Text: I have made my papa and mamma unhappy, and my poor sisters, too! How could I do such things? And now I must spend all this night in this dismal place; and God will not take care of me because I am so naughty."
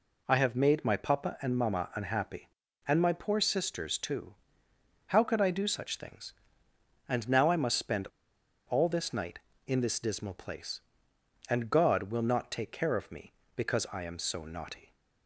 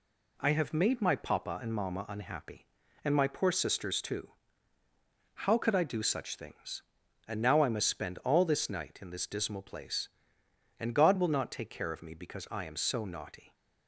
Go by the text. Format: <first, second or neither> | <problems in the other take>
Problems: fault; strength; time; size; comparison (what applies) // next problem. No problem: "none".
second | pauses between "spend" and "all"; noticeable; at 8.0 s; 0.62 s long